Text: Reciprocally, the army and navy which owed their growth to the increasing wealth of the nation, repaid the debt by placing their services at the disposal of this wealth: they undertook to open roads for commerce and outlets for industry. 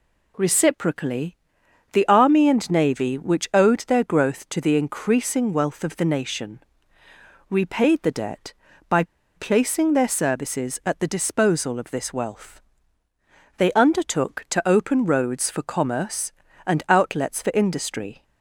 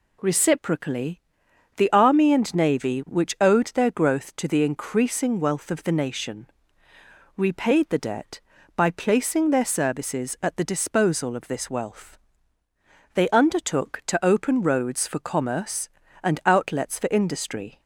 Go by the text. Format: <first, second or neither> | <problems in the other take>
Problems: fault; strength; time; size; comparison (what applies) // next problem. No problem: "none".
second | pauses between "by" and "placing"; slight; at 9.0 s; 0.33 s long